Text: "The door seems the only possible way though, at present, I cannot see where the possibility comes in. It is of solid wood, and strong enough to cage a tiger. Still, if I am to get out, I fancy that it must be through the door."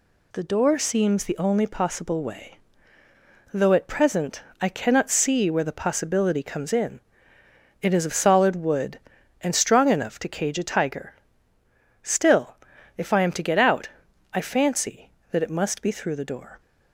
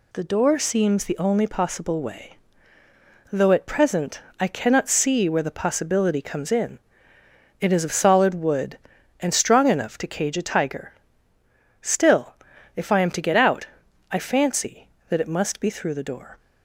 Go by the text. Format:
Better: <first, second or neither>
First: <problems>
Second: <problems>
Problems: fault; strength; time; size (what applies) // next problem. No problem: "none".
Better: neither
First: pauses between "way" and "though"; noticeable; at 2.5 s; 0.96 s long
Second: pauses between "way" and "though"; noticeable; at 2.3 s; 0.96 s long